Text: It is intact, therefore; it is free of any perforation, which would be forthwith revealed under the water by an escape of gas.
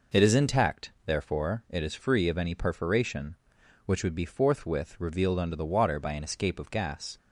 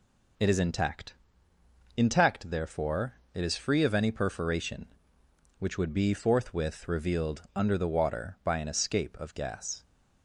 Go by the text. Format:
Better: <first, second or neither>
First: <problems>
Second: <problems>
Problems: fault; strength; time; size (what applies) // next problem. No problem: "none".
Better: first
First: none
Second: says "intact" twice; at 1.9 s